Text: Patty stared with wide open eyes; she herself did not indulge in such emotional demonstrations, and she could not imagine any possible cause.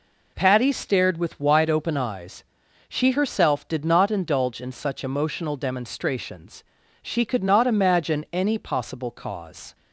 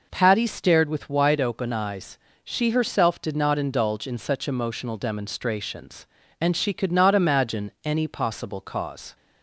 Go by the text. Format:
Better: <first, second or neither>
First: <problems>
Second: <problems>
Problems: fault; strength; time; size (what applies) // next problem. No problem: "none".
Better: second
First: skips "and"; at 6.8 s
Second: none